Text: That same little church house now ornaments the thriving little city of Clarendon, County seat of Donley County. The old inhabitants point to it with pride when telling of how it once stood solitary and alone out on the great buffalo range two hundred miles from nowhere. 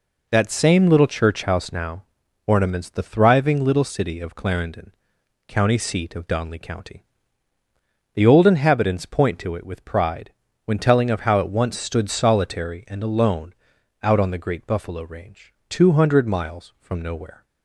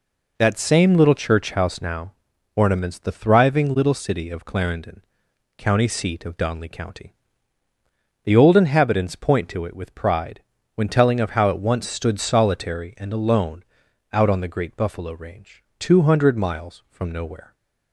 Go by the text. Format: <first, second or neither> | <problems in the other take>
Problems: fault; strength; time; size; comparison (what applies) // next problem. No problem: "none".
neither | pauses between "now" and "ornaments"; noticeable; the same in both // pauses between "pride" and "when"; slight; the same in both // pauses between "alone" and "out"; noticeable; the same in both // pauses between "range" and "two"; slight; the same in both